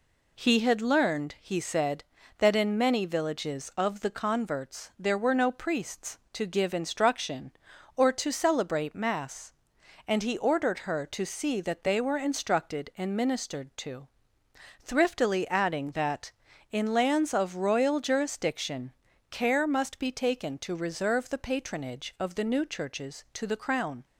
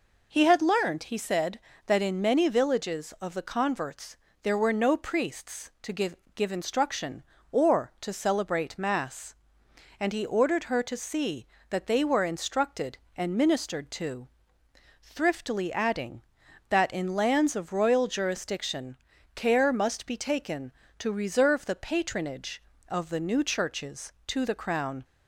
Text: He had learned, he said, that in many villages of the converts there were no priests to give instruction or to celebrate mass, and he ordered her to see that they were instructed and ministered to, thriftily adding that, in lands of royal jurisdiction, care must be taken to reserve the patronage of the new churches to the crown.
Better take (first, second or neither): first